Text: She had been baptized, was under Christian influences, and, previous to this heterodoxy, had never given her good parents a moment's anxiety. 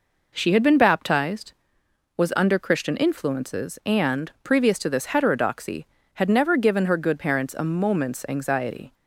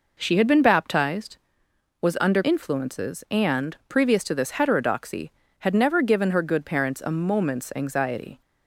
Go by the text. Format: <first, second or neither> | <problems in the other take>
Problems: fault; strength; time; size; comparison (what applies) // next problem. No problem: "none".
first | skips "Christian"; at 2.4 s